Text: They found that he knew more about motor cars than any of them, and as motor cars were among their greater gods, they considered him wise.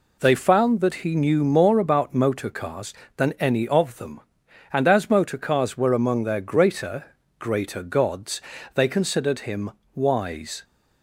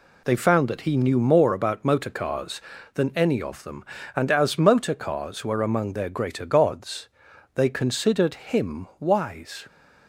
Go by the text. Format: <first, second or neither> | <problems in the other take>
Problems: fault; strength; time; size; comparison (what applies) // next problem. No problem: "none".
second | says "greater" twice; at 7.3 s // pauses between "him" and "wise"; slight; at 9.6 s; 0.24 s long